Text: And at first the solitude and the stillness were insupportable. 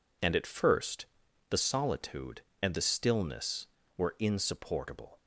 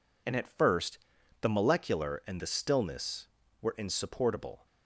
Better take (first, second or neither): first